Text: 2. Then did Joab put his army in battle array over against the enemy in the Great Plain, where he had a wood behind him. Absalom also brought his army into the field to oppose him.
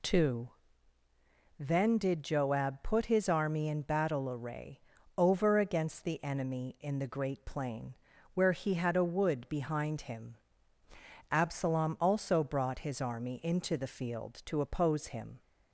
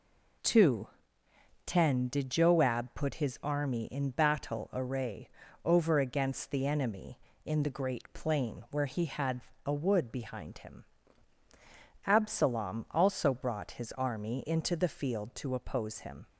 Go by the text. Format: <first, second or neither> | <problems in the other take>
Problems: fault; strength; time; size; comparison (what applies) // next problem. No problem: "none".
first | says "Ten" for "Then"; at 1.6 s // pauses between "array" and "over"; at 5.2 s; 0.38 s long; slight in the first // pauses between "had" and "a"; slight; at 9.4 s; 0.24 s long